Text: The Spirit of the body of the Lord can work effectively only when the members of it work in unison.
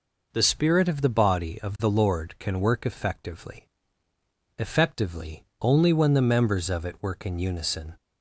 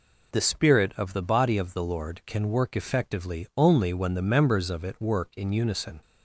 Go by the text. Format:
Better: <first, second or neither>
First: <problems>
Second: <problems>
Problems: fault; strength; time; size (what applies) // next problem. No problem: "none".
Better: second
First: says "effectively" twice; at 4.5 s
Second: none